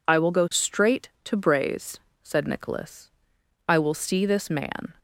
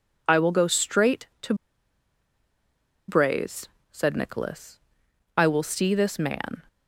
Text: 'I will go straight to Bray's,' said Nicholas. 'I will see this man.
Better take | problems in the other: first | pauses between "to" and "Bray's"; strong; at 1.5 s; 1.5 s long

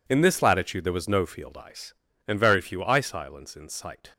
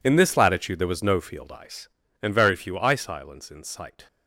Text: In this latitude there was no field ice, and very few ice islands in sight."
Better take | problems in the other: first | gets quieter; strong; throughout; 16.5 dB

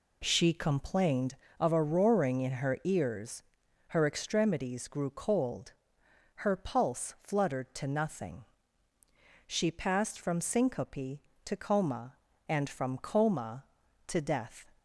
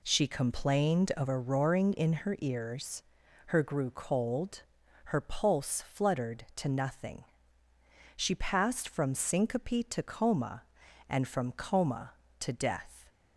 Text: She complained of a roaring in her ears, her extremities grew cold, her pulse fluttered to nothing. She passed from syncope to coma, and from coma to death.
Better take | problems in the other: first | skips "extremities"; at 3.6 s

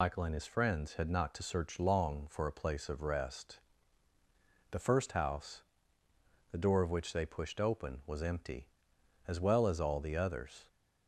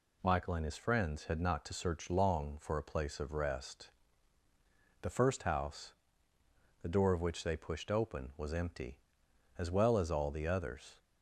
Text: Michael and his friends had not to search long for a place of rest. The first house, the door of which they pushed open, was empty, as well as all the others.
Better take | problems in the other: second | loses the start of "Michael"; at 0.0 s; 100 ms

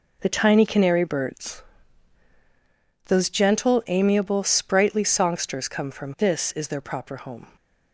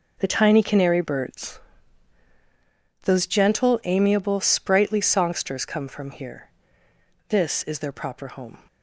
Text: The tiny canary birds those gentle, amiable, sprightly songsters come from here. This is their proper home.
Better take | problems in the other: second | pauses between "birds" and "those"; strong; at 1.6 s; 1.4 s long; strong in the second // skips "here"; at 6.1 s

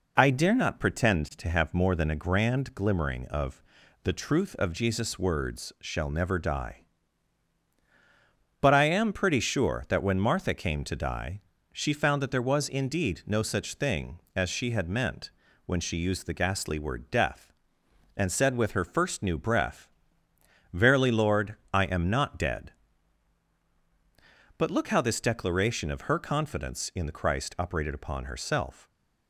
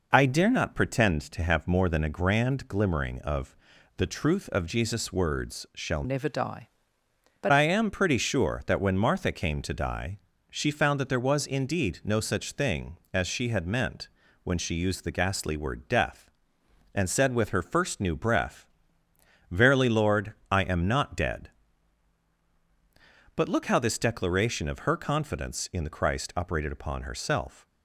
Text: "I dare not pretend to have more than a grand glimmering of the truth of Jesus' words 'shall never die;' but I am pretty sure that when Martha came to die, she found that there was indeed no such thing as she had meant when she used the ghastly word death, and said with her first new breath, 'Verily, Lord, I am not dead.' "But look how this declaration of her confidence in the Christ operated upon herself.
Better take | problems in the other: first | pauses between "of" and "the"; at 3.5 s; 0.40 s long; also in the first // changes voice from "never" to "but"; from 6.0 to 7.5 s; 1.5 s long // pauses between "meant" and "when"; slight; at 14.0 s; 0.36 s long; slight in the first

